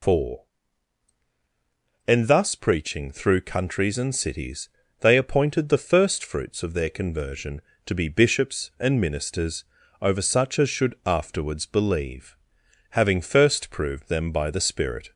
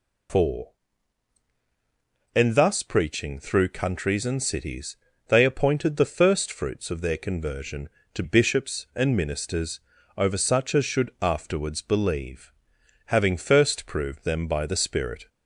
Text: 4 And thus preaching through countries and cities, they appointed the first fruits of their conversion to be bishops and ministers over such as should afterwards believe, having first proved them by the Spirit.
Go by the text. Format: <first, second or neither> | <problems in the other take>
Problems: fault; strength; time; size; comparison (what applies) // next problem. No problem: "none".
first | skips "be"; at 8.2 s // pauses between "ministers" and "over"; at 9.7 s; 0.38 s long; also in the first